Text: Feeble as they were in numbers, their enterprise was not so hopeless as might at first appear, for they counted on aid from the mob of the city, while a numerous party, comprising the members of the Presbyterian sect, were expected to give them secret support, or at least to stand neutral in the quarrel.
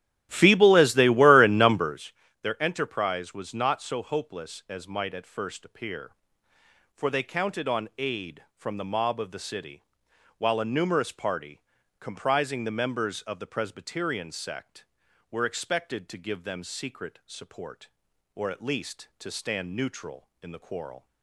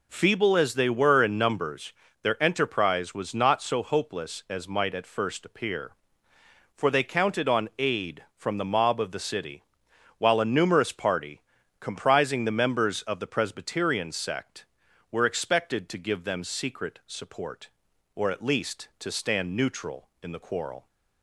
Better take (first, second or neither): second